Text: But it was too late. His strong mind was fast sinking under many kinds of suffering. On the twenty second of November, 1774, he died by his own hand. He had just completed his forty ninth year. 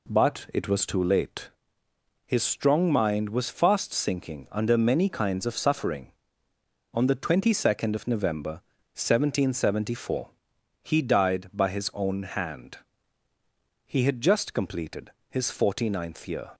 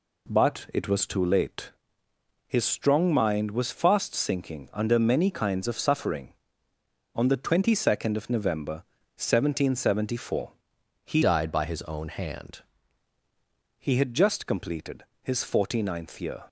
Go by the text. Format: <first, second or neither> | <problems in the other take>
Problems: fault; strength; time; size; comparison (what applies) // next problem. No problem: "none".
first | changes voice from "died" to "hand"; from 11.2 to 12.6 s; 1.4 s long // pauses between "completed" and "his"; slight; at 15.0 s; 0.18 s long; slight in the first